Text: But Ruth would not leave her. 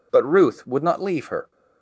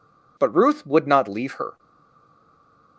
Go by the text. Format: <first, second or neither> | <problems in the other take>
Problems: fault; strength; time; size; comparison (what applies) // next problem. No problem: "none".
first | stays silent after the last word; noticeable; from 1.7 s on; 1.2 s long